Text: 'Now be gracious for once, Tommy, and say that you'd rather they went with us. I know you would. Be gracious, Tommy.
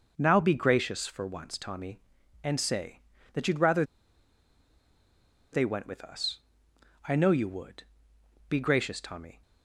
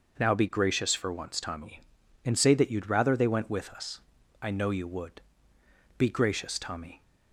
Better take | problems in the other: second | pauses between "rather" and "they"; strong; at 3.8 s; 1.6 s long

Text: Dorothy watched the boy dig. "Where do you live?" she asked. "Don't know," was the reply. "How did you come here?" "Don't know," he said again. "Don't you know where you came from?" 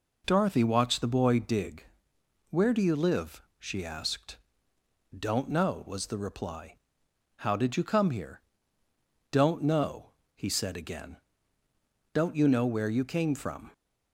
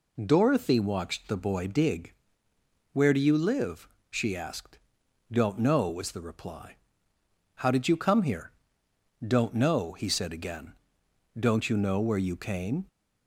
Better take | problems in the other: first | stops before "from"; at 12.8 s

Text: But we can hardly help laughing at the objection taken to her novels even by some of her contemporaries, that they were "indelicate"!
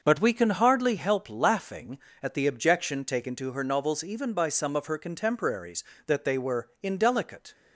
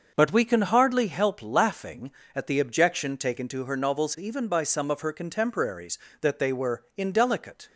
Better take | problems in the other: neither | starts louder than the rest; the same in both

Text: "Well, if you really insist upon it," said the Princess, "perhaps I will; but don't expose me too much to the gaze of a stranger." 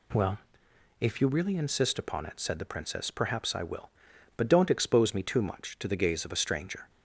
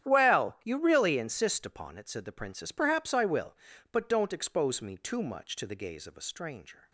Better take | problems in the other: first | starts louder than the rest; strong; until 1.1 s; 10 dB // skips "if"; at 0.6 s

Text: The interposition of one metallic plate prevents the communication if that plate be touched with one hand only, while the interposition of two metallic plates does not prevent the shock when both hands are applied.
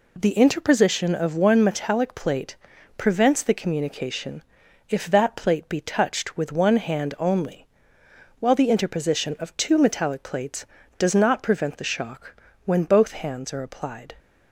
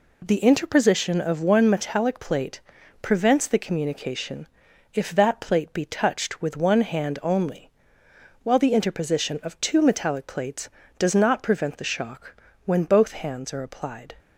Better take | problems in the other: neither | pauses between "plate" and "prevents"; the same in both // pauses between "communication" and "if"; noticeable; the same in both // pauses between "shock" and "when"; slight; the same in both

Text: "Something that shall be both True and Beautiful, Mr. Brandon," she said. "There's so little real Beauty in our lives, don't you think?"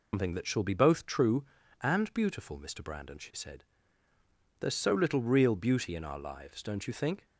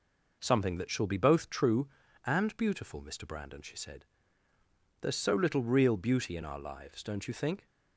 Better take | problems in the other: second | loses the start of "Something"; at 0.1 s; 160 ms

